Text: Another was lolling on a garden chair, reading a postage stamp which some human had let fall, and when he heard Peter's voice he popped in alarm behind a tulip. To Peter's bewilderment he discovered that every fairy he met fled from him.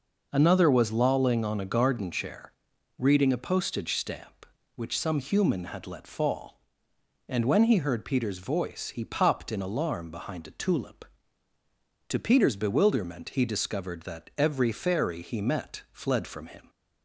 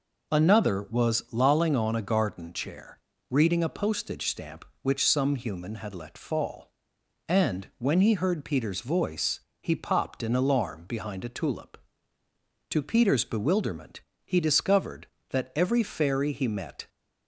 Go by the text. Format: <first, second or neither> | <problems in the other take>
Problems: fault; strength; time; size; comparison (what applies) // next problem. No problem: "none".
first | pauses between "voice" and "he"; slight; at 9.4 s; 0.22 s long // pauses between "bewilderment" and "he"; slight; at 14.0 s; 0.26 s long // stops before "fled from him"; at 16.8 s